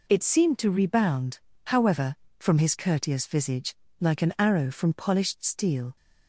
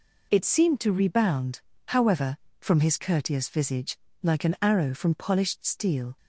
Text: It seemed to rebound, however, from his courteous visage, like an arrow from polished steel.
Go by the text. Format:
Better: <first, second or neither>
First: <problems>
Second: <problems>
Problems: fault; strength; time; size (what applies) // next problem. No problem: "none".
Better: neither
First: none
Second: none